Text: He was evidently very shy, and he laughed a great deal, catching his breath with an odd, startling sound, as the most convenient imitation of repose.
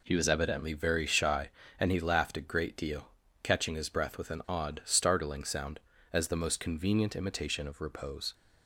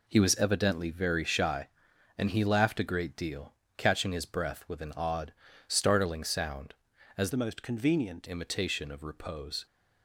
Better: first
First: none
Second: changes voice from "the" to "convenient"; from 7.3 to 8.2 s; 0.9 s long

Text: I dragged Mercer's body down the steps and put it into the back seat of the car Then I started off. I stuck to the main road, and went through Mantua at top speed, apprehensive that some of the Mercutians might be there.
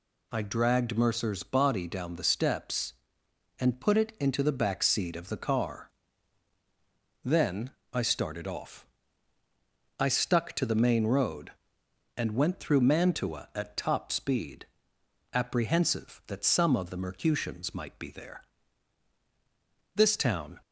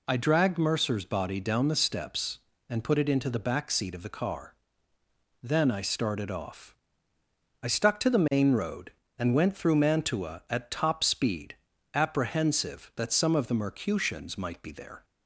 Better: second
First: pauses between "car" and "Then"; strong; at 5.9 s; 1.3 s long // pauses between "Then" and "I"; slight; at 7.7 s; 0.22 s long // goes on to say "This town"; noticeable; from 19.9 s on; 0.64 s long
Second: pauses between "car" and "Then"; noticeable; at 4.5 s; 0.88 s long

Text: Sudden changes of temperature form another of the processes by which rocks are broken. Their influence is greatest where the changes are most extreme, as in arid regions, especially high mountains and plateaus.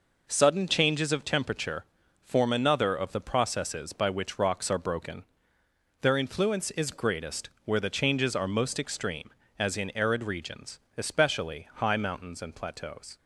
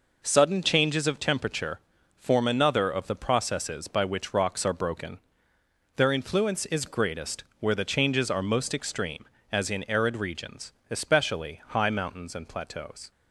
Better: neither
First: pauses between "temperature" and "form"; slight; at 1.8 s; 0.36 s long // pauses between "greatest" and "where"; slight; at 7.4 s; 0.15 s long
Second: pauses between "temperature" and "form"; slight; at 1.8 s; 0.36 s long // pauses between "greatest" and "where"; slight; at 7.4 s; 0.16 s long

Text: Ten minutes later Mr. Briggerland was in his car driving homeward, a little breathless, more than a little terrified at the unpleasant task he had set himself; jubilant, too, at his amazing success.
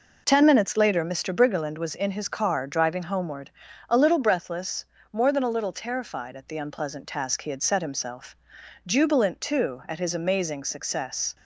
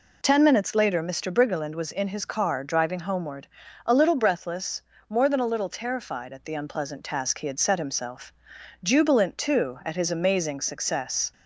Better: second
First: gets quieter; throughout; 6.5 dB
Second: none

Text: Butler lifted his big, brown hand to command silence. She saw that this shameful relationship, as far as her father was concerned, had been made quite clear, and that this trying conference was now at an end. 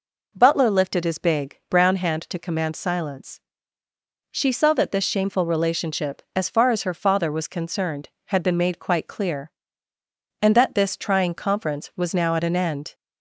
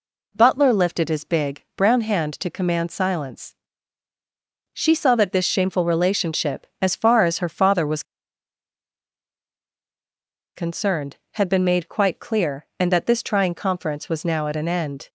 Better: first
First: none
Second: pauses between "was" and "concerned"; strong; at 8.0 s; 2.5 s long

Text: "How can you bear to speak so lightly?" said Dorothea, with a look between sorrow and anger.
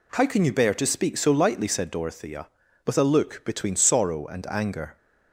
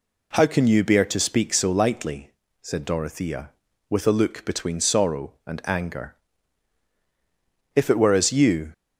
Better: first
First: none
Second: goes on to say "If it were as you"; noticeable; from 7.7 s on; 0.96 s long

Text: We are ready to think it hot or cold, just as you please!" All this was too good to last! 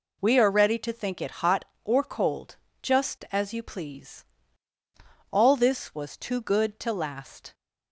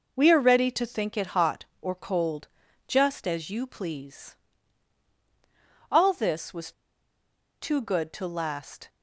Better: first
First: none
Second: pauses between "was" and "too"; noticeable; at 6.7 s; 0.90 s long

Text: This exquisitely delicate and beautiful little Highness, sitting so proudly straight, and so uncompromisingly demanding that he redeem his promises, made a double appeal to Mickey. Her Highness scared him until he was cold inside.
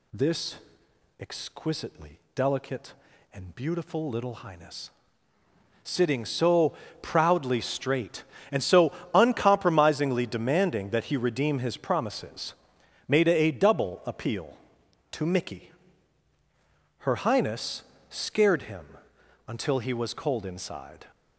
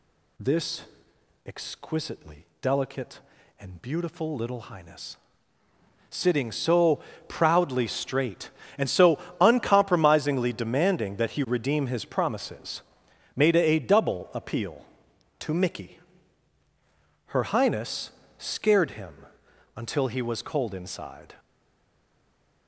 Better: first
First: pauses between "This" and "exquisitely"; noticeable; at 0.5 s; 0.64 s long // pauses between "exquisitely" and "delicate"; slight; at 2.1 s; 0.16 s long // pauses between "so" and "proudly"; slight; at 6.7 s; 0.28 s long // pauses between "so" and "uncompromisingly"; slight; at 8.9 s; 0.24 s long // pauses between "Highness" and "scared"; slight; at 17.8 s; 0.25 s long // pauses between "him" and "until"; noticeable; at 18.9 s; 0.50 s long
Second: pauses between "This" and "exquisitely"; noticeable; at 0.8 s; 0.64 s long // pauses between "exquisitely" and "delicate"; slight; at 2.4 s; 0.16 s long // pauses between "so" and "proudly"; slight; at 6.9 s; 0.28 s long // pauses between "so" and "uncompromisingly"; slight; at 9.1 s; 0.24 s long // pauses between "Highness" and "scared"; slight; at 18.1 s; 0.26 s long // pauses between "him" and "until"; noticeable; at 19.2 s; 0.50 s long // stays silent after the last word; noticeable; from 21.3 s on; 1.3 s long

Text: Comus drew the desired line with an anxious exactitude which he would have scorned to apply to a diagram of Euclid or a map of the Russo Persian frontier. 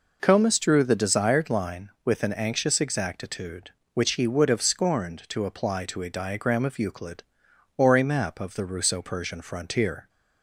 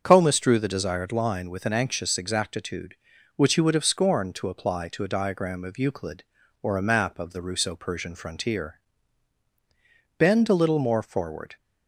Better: first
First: none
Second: starts louder than the rest; until 1.0 s; 7 dB // goes on to say "Bend a little more forward"; from 10.1 s on; 1.3 s long

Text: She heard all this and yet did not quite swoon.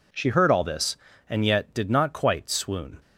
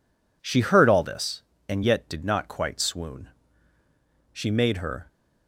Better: first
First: none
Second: goes on to say "She made her"; noticeable; from 4.3 s on; 0.74 s long

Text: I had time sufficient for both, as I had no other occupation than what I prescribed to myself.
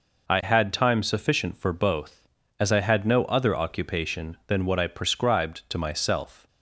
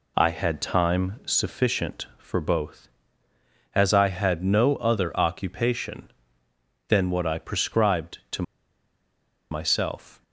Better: first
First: none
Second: pauses between "to" and "myself"; at 8.4 s; 1.0 s long

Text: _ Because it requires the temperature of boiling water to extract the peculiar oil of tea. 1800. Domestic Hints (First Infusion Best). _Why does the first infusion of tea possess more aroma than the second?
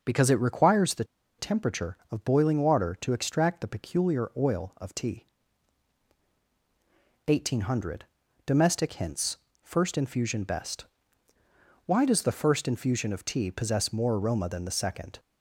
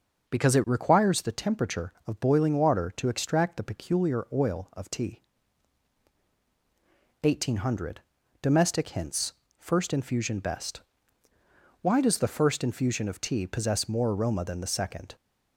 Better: second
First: starts louder than the rest; noticeable; until 1.0 s; 6 dB // pauses between "the" and "temperature"; slight; at 1.0 s; 0.34 s long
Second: starts louder than the rest; noticeable; until 1.3 s; 6 dB

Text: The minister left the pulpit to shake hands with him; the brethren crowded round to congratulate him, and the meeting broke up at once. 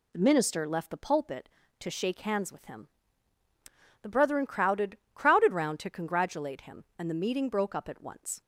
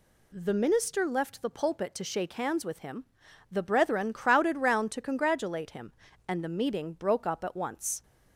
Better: second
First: says "crowded" twice; at 5.1 s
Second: none

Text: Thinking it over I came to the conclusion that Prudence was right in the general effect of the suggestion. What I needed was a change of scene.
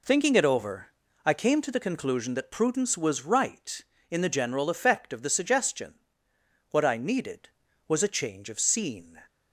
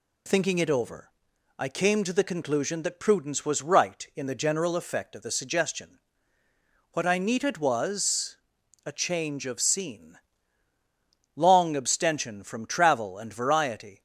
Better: first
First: pauses between "over" and "I"; slight; at 0.8 s; 0.36 s long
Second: pauses between "over" and "I"; noticeable; at 1.1 s; 0.46 s long // pauses between "was" and "a"; noticeable; at 8.3 s; 0.50 s long // goes on to say "Long abstention from travel and variety"; strong; from 11.3 s on; 2.6 s long

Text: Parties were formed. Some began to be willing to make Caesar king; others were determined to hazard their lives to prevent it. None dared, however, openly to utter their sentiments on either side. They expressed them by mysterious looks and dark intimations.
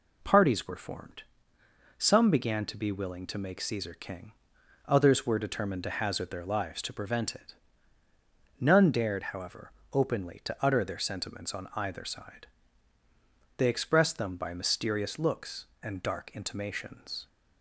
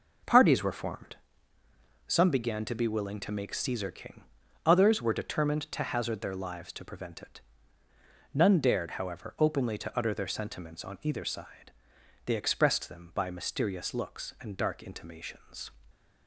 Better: first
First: none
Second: starts louder than the rest; noticeable; until 1.5 s; 5 dB

